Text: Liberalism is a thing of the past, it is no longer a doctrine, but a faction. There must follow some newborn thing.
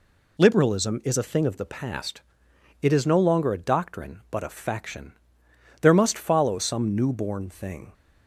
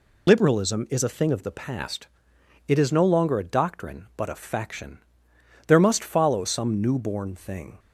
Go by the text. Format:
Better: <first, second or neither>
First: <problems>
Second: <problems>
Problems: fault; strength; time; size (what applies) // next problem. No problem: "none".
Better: first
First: none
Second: loses the start of "Liberalism"; at 0.2 s; 25 ms